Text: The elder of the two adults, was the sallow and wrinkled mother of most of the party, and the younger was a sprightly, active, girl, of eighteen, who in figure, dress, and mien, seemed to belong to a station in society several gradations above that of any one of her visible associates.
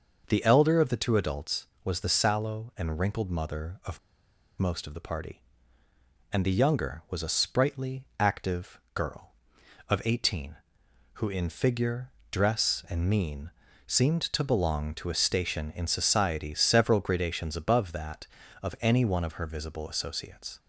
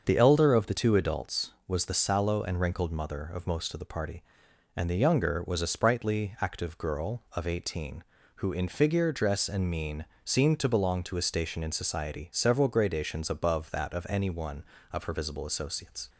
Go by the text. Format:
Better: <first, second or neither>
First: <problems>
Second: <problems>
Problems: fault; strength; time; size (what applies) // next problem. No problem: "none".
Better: second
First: starts louder than the rest; noticeable; until 1.2 s; 6 dB // pauses between "of" and "most"; noticeable; at 3.9 s; 0.61 s long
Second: starts louder than the rest; until 1.0 s; 6.5 dB